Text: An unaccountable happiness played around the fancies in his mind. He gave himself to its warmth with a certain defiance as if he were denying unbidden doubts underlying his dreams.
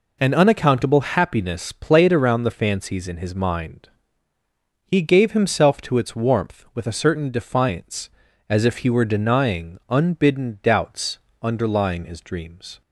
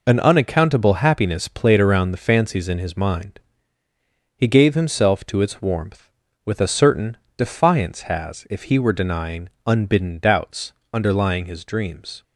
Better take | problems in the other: first | pauses between "certain" and "defiance"; slight; at 7.1 s; 0.20 s long // says "has" for "as"; at 8.0 s // pauses between "denying" and "unbidden"; slight; at 9.4 s; 0.18 s long // pauses between "doubts" and "underlying"; slight; at 10.7 s; 0.20 s long; slight in the first

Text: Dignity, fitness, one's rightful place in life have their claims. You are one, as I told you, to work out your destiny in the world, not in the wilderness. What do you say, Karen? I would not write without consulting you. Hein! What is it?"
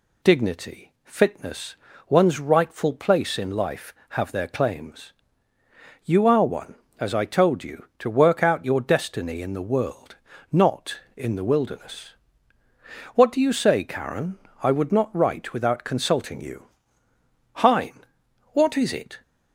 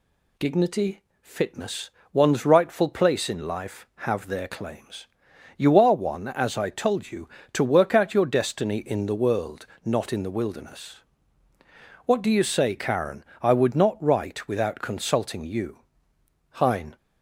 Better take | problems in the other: first | stops before "What is it"; at 16.9 s

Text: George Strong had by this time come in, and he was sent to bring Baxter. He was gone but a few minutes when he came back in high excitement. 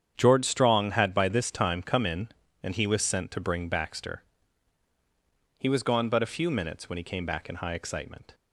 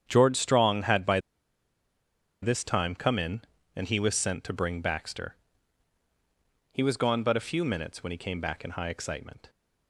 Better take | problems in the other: first | starts louder than the rest; strong; until 1.0 s; 8.5 dB; strong in the first // pauses between "by" and "this"; at 1.2 s; 1.2 s long

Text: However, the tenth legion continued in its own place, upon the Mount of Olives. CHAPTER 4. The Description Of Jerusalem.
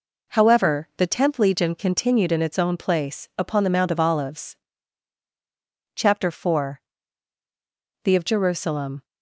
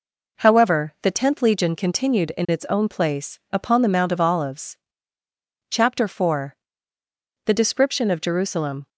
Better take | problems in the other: second | skips "Description"; at 8.1 s

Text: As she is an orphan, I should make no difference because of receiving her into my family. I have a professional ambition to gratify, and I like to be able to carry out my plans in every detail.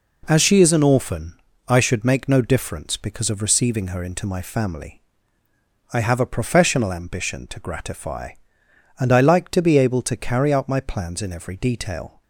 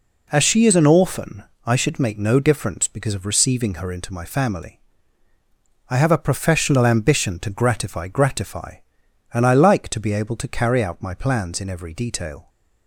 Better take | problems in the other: first | says "gratify" twice; at 8.0 s

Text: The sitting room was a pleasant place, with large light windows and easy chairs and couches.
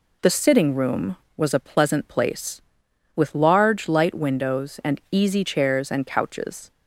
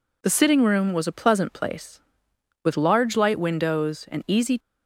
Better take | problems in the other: first | stops before "chairs and couches"; at 4.5 s

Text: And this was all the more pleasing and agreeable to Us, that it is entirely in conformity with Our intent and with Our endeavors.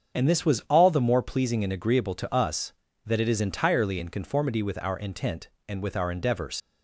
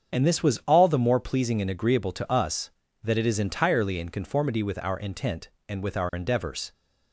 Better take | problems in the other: second | starts louder than the rest; until 1.2 s; 7 dB; strong in the second // leaves "endeavors" unfinished; at 6.6 s; 80 ms

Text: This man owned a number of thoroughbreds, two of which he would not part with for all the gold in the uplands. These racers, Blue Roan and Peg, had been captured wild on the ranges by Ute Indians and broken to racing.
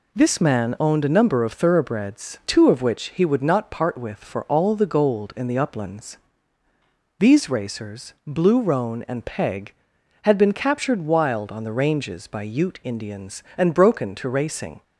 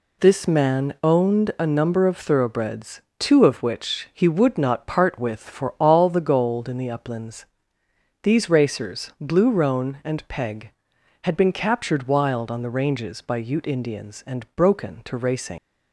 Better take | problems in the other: first | leaves "racing" unfinished; at 15.5 s; 85 ms

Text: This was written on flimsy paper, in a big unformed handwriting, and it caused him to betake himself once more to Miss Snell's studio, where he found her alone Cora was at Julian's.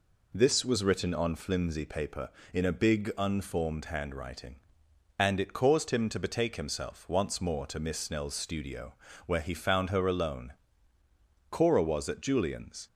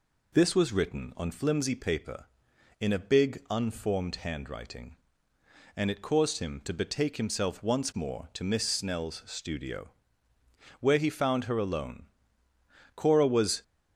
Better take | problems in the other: first | pauses between "alone" and "Cora"; noticeable; at 12.0 s; 0.88 s long; noticeable in the first // stops before "at Julian's"; at 13.6 s

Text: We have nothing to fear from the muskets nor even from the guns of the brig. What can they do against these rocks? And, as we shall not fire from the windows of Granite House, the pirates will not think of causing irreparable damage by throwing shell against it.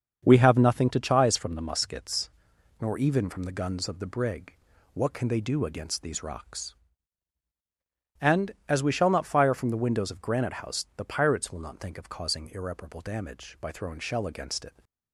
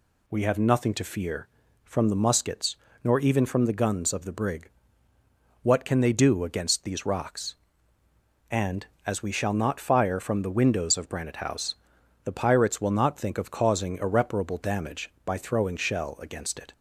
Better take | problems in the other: second | starts louder than the rest; until 1.2 s; 7 dB // says "chise" for "fear"; at 1.0 s // pauses between "muskets" and "nor"; noticeable; at 2.2 s; 0.50 s long; slight in the second

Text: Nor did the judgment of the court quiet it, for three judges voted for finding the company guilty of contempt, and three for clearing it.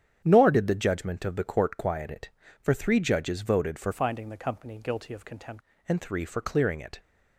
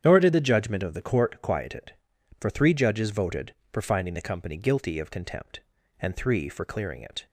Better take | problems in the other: second | starts louder than the rest; strong; until 1.2 s; 9 dB; strong in the second // changes voice from "finding" to "contempt"; from 3.9 to 5.6 s; 1.7 s long

